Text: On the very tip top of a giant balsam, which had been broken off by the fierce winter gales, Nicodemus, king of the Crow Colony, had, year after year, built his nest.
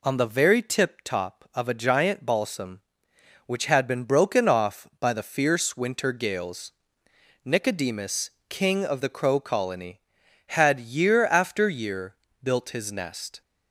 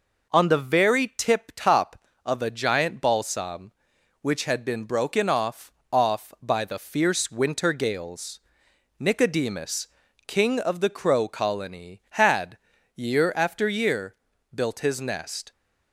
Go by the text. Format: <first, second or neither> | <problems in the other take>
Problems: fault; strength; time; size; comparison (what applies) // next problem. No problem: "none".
first | says "off" twice; at 5.9 s